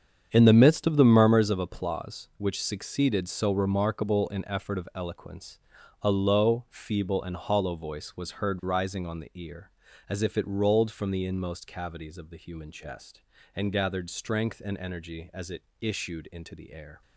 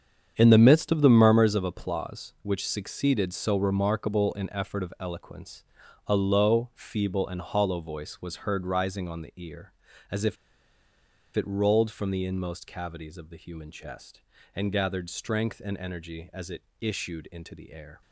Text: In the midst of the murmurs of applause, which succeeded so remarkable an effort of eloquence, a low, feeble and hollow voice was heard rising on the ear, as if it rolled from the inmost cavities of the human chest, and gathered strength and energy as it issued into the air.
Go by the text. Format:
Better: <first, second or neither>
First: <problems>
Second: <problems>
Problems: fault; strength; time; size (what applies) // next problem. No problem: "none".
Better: first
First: starts louder than the rest; strong; until 1.3 s; 8 dB // pauses between "it" and "issued"; slight; at 15.6 s; 0.18 s long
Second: starts louder than the rest; strong; until 1.3 s; 7.5 dB // pauses between "if" and "it"; at 10.3 s; 1.0 s long // pauses between "it" and "issued"; slight; at 16.6 s; 0.18 s long